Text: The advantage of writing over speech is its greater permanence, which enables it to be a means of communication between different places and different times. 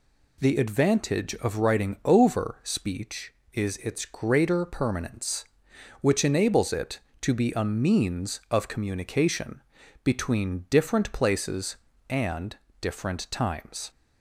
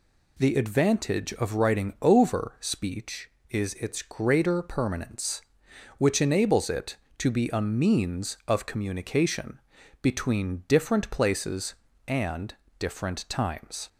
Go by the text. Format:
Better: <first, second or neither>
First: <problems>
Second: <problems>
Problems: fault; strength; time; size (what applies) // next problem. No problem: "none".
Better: neither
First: pauses between "communication" and "between"; at 9.6 s; 0.42 s long // pauses between "and" and "different"; slight; at 12.5 s; 0.24 s long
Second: pauses between "communication" and "between"; at 9.5 s; 0.42 s long // pauses between "and" and "different"; slight; at 12.5 s; 0.24 s long